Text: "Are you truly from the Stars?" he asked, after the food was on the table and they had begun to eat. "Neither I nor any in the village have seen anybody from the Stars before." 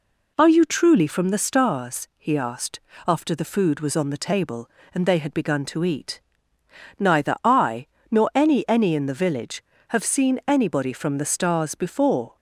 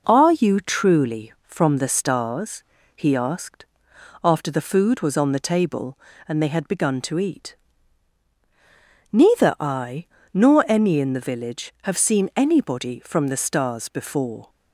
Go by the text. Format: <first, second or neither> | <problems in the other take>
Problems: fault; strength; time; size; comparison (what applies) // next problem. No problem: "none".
second | pauses between "I" and "nor"; slight; at 7.8 s; 0.26 s long; slight in the second // says "any" twice; at 8.6 s